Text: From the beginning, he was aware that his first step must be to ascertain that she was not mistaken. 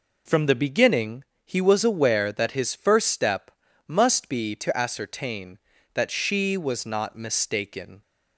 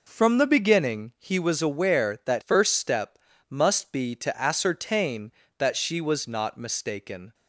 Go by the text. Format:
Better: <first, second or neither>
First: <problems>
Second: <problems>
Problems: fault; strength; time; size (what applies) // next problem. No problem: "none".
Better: first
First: pauses between "step" and "must"; at 3.4 s; 0.38 s long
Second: skips "his"; at 2.4 s // pauses between "step" and "must"; slight; at 3.1 s; 0.32 s long